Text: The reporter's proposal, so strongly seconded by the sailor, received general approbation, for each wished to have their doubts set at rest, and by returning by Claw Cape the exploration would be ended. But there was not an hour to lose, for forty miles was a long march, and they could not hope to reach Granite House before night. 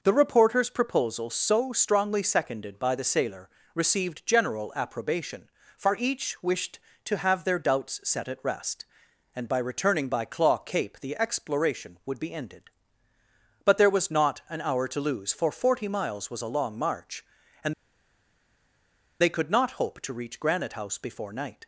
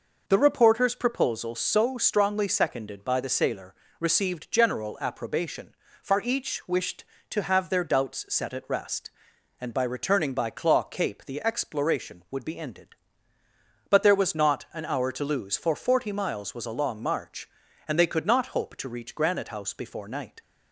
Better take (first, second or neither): second